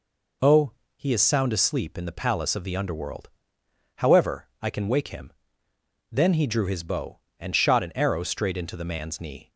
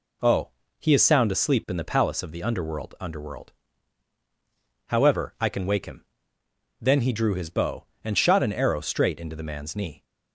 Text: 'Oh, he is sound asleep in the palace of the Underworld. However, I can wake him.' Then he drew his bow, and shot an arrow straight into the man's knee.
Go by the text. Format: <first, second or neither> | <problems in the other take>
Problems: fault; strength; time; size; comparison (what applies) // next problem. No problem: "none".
first | says "Underworld" twice; at 2.9 s